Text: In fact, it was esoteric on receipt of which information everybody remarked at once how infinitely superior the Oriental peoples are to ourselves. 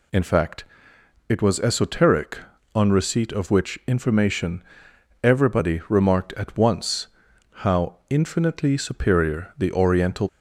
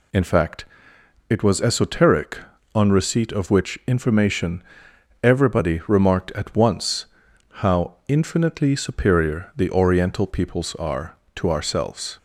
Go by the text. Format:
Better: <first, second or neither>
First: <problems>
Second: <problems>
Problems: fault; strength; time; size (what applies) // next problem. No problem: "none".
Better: second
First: pauses between "information" and "everybody"; noticeable; at 4.6 s; 0.60 s long // pauses between "once" and "how"; noticeable; at 7.0 s; 0.52 s long // stops before "peoples are to ourselves"; at 10.2 s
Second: pauses between "information" and "everybody"; noticeable; at 4.6 s; 0.60 s long // pauses between "once" and "how"; noticeable; at 7.0 s; 0.52 s long